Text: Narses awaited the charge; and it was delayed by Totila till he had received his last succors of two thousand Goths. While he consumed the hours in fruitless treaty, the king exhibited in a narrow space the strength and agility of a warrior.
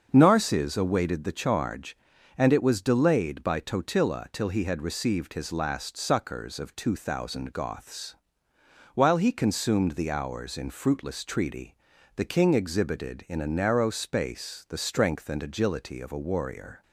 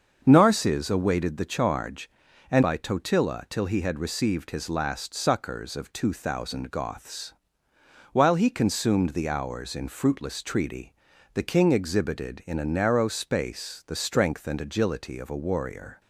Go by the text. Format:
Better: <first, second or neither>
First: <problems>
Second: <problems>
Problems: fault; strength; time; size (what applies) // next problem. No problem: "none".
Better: first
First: starts louder than the rest; until 1.1 s; 6.5 dB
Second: starts louder than the rest; until 1.2 s; 6.5 dB // skips "it was delayed"; at 2.6 s